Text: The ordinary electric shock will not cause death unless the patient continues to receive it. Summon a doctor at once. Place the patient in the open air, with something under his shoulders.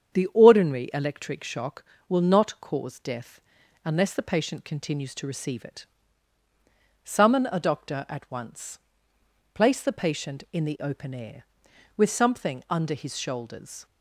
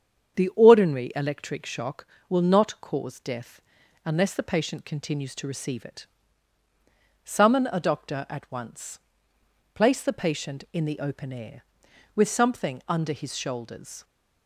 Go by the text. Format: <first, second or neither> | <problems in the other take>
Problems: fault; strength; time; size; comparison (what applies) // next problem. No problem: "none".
neither | starts louder than the rest; strong; the same in both // pauses between "death" and "unless"; the same in both